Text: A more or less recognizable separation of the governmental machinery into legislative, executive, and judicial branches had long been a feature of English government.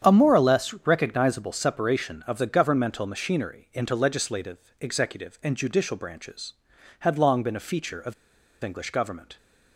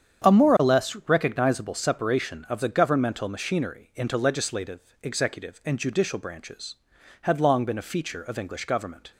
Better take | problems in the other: second | starts louder than the rest; strong; until 1.1 s; 8.5 dB; strong in the second // pauses between "of" and "English"; noticeable; at 8.1 s; 0.50 s long

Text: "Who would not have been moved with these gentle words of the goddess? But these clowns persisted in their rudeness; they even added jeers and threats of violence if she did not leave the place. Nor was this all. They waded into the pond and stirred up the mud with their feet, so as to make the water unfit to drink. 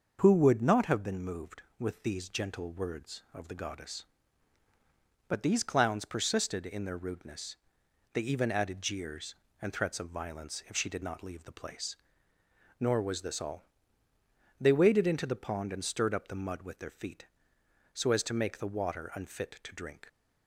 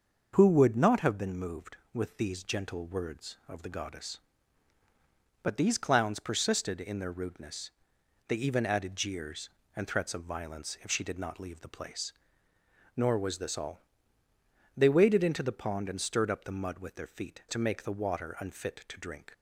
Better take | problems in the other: first | starts louder than the rest; until 1.3 s; 6.5 dB; also in the first // skips "so as"; at 17.4 s

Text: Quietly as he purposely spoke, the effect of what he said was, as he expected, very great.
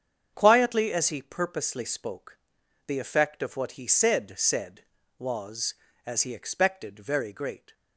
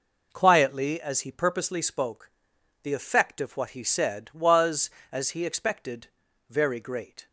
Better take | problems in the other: second | starts louder than the rest; strong; until 1.3 s; 7.5 dB // says "said" twice; at 4.3 s

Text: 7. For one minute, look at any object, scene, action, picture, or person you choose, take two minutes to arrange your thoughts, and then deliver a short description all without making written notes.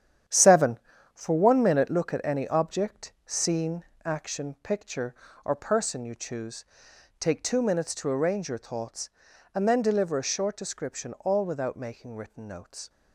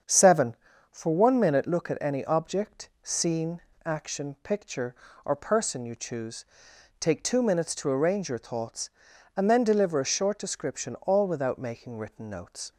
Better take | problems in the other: second | gets quieter; strong; throughout; 8.5 dB // starts louder than the rest; strong; until 1.6 s; 9.5 dB; strong in the second

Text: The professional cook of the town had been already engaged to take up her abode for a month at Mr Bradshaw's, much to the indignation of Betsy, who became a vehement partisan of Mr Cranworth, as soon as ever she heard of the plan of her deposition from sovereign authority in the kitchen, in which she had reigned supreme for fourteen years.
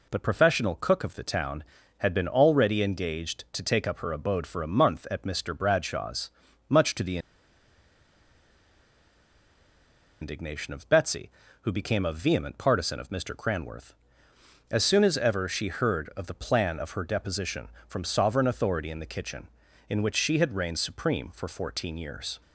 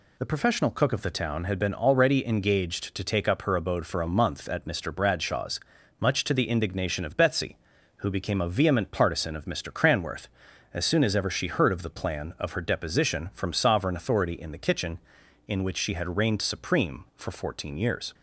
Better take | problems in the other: second | pauses between "the" and "indignation"; strong; at 7.1 s; 3.0 s long

